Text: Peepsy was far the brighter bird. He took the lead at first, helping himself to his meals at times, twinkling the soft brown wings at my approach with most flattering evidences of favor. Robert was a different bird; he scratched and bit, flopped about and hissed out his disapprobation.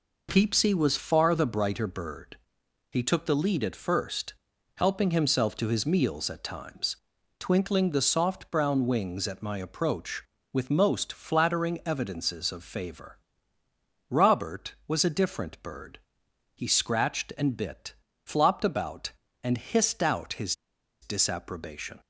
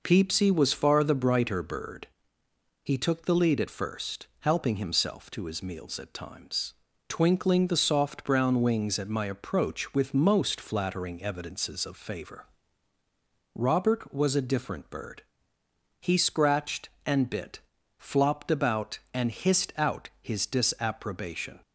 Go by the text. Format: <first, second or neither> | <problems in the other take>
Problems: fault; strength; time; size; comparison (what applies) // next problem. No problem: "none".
second | pauses between "his" and "disapprobation"; noticeable; at 20.5 s; 0.48 s long